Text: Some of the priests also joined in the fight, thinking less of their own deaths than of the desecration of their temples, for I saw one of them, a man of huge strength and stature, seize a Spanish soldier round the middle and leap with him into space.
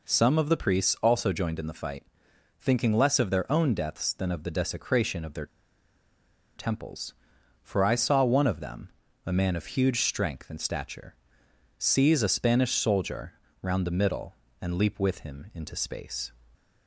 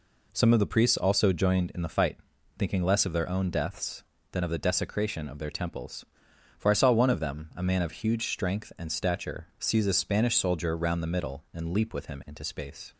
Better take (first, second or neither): second